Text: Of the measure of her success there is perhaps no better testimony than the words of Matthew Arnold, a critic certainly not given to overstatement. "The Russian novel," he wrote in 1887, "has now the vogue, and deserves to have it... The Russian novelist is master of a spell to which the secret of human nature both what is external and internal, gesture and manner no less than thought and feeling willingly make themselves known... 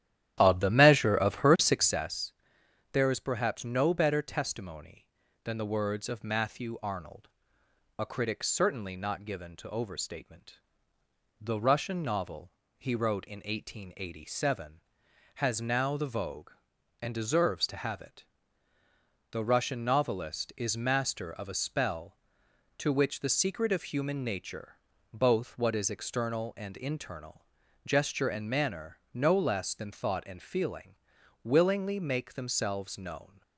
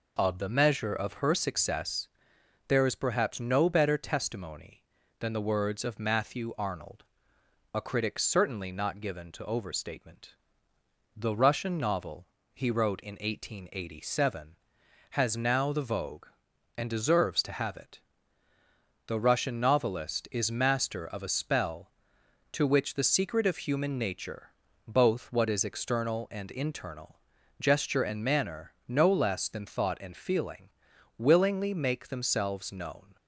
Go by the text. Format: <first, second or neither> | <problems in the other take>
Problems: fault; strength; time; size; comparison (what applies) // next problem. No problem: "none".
second | starts louder than the rest; strong; until 2.0 s; 12 dB // pauses between "success" and "there"; noticeable; at 2.3 s; 0.62 s long; noticeable in the second // pauses between "nature" and "both"; slight; at 24.7 s; 0.36 s long; slight in the second // pauses between "manner" and "no"; slight; at 28.9 s; 0.16 s long; slight in the second // pauses between "feeling" and "willingly"; noticeable; at 30.9 s; 0.48 s long; noticeable in the second